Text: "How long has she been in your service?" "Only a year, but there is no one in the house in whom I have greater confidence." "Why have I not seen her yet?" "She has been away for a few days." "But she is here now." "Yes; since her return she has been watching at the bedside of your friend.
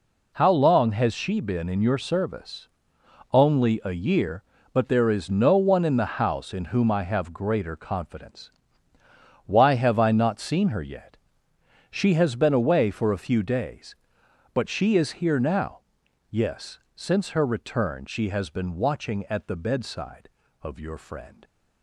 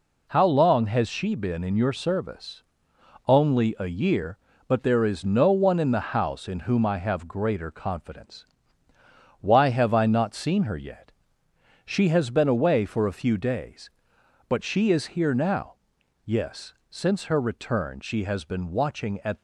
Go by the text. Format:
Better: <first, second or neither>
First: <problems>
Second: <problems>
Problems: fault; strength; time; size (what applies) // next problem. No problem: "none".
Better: first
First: none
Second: stops before "the bedside of your friend"; at 19.3 s